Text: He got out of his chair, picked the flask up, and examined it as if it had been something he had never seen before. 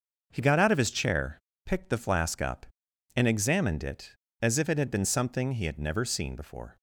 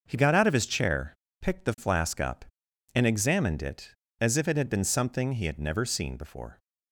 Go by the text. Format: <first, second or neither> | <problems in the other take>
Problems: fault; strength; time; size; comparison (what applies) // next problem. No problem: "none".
neither | starts louder than the rest; noticeable; the same in both